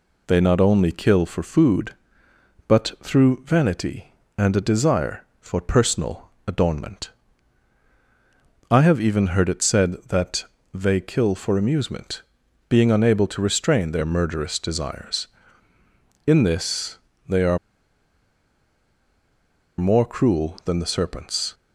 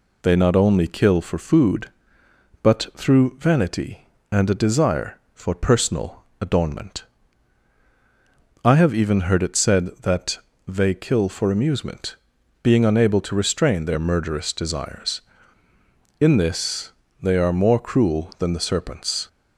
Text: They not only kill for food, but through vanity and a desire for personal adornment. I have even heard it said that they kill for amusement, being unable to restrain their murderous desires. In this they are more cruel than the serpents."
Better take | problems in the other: second | pauses between "personal" and "adornment"; slight; at 6.2 s; 0.16 s long; slight in the second // pauses between "that" and "they"; slight; at 10.4 s; 0.28 s long; slight in the second // pauses between "this" and "they"; slight; at 16.9 s; 0.30 s long; slight in the second // pauses between "are" and "more"; strong; at 17.5 s; 2.2 s long

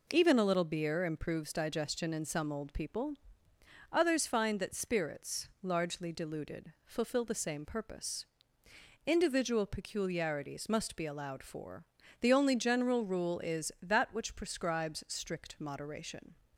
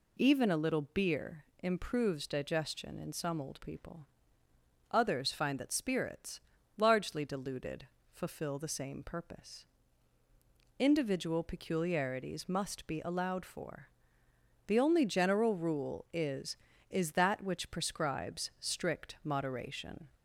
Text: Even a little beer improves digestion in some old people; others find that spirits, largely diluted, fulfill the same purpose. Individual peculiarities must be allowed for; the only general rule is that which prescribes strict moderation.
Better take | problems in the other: first | pauses between "beer" and "improves"; slight; at 1.4 s; 0.18 s long // says "is" twice; at 16.8 s

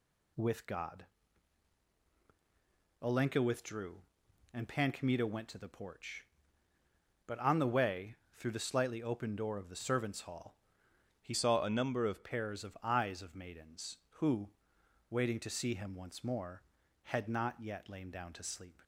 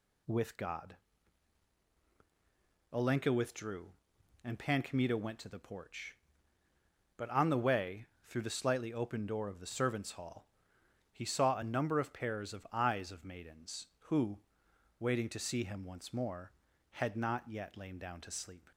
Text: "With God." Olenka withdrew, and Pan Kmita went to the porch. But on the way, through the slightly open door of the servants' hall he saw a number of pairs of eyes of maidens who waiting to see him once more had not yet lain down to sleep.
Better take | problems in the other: second | pauses between "hall" and "he"; noticeable; at 10.5 s; 0.64 s long; noticeable in the second // changes voice from "saw" to "of"; from 11.3 to 12.2 s; 0.9 s long // pauses between "who" and "waiting"; noticeable; at 14.5 s; 0.58 s long; noticeable in the second

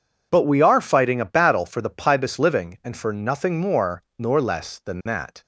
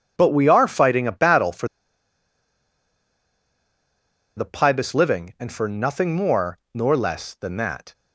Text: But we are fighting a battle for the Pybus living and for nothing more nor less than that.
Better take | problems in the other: first | pauses between "for" and "the"; strong; at 1.6 s; 2.6 s long // pauses between "more" and "nor"; slight; at 6.5 s; 0.16 s long; slight in the first

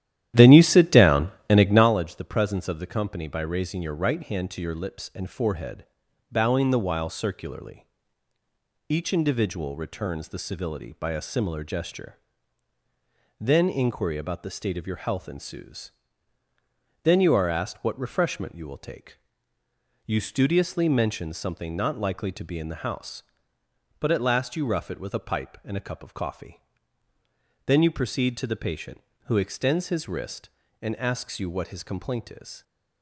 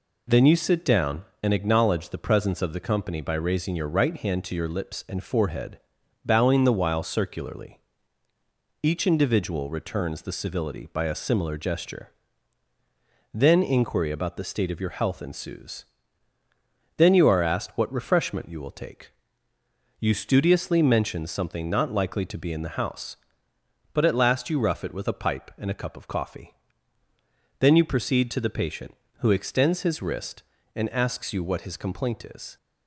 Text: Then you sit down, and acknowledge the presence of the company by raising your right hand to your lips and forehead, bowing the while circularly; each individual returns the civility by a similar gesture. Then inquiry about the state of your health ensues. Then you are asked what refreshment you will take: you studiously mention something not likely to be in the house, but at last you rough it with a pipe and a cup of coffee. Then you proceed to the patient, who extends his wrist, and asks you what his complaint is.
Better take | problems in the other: second | starts louder than the rest; strong; until 1.9 s; 12 dB

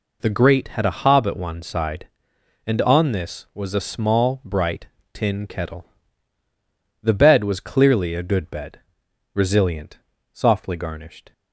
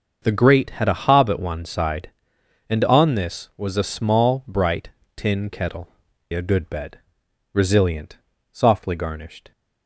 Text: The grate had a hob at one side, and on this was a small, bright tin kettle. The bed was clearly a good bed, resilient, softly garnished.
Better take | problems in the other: first | starts louder than the rest; until 1.2 s; 6.5 dB // pauses between "bright" and "tin"; slight; at 4.8 s; 0.28 s long; slight in the first // skips "The bed was clearly"; at 6.1 s

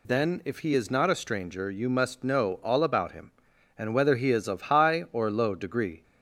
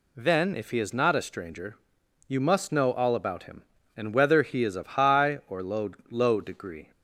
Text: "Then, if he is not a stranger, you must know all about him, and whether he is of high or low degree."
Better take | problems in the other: first | says "low" twice; at 6.1 s

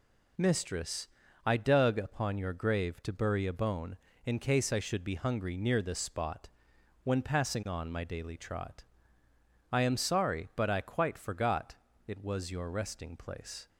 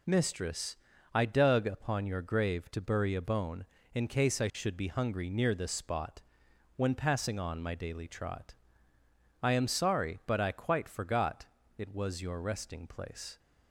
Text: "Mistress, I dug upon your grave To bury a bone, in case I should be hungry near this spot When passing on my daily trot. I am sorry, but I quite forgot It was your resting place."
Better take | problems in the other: neither | pauses between "spot" and "When"; noticeable; the same in both // pauses between "forgot" and "It"; slight; the same in both

